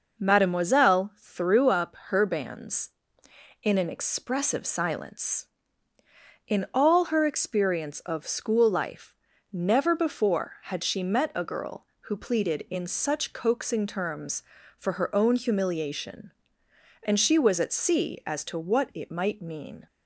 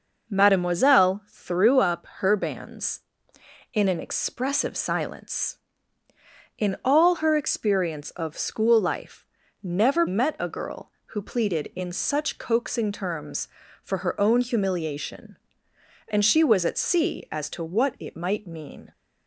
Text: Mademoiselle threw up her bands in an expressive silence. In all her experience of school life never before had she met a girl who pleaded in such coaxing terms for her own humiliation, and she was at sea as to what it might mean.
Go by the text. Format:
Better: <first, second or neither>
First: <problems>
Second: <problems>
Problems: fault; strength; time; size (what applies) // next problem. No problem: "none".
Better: first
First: pauses between "life" and "never"; at 9.1 s; 0.38 s long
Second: pauses between "life" and "never"; at 9.2 s; 0.38 s long // skips "before had she"; at 10.0 s